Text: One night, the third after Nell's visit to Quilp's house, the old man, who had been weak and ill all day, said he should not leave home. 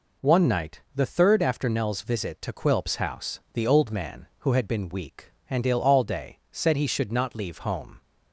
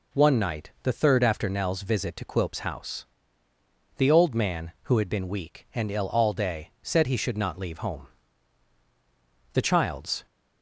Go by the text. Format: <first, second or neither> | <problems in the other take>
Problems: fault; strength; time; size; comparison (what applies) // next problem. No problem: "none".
first | goes on to say "The child's"; noticeable; from 9.5 s on; 0.72 s long